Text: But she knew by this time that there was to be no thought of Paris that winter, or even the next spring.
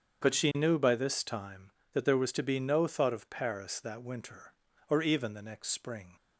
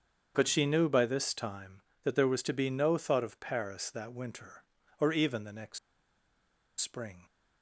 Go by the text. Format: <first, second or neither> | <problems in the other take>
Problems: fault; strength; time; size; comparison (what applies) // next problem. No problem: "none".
first | starts louder than the rest; strong; until 1.3 s; 7.5 dB; strong in the first // pauses between "next" and "spring"; at 5.7 s; 1.0 s long